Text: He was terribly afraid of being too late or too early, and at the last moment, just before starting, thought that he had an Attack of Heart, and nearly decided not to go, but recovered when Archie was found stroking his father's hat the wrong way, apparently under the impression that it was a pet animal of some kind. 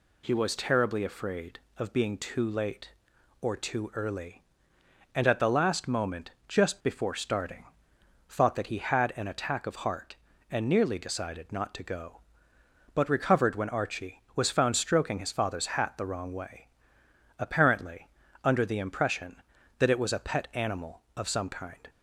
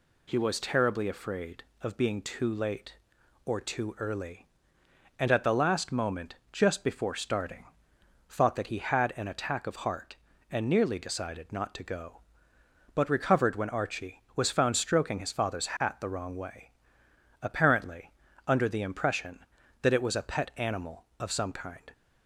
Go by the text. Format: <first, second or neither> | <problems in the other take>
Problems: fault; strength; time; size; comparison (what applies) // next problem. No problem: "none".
neither | pauses between "apparently" and "under"; slight; the same in both